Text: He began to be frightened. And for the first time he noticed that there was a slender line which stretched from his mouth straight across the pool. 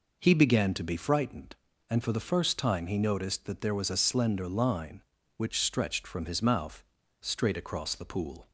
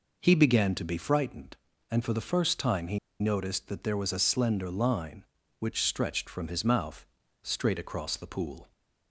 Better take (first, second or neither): first